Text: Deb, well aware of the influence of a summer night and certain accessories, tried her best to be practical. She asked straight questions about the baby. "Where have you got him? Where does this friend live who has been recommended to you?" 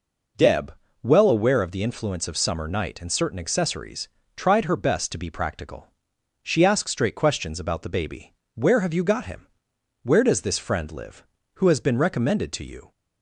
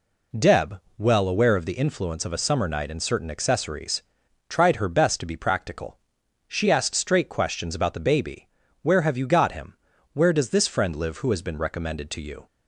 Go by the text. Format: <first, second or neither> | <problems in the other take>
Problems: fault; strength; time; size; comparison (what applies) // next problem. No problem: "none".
second | skips "a"; at 2.3 s